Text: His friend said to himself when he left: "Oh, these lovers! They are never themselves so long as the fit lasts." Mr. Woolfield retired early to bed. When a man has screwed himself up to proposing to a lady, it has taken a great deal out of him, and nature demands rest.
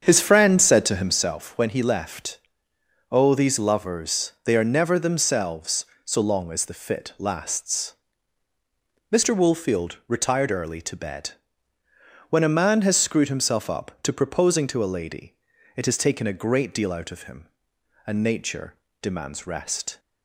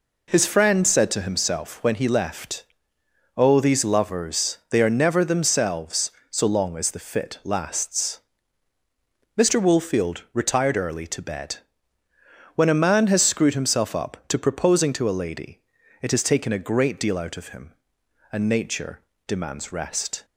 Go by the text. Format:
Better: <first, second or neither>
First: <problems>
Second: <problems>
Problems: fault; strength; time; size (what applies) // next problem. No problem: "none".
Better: second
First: starts louder than the rest; strong; until 1.4 s; 7.5 dB // pauses between "nature" and "demands"; slight; at 18.7 s; 0.26 s long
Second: pauses between "nature" and "demands"; slight; at 18.9 s; 0.26 s long